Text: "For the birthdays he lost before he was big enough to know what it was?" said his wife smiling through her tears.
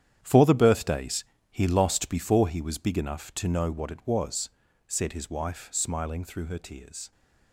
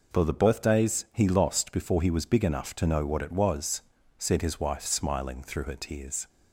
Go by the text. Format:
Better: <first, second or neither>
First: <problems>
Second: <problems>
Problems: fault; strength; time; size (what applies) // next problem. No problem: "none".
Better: second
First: gets quieter; strong; throughout; 12 dB // pauses between "birthdays" and "he"; slight; at 1.2 s; 0.26 s long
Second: none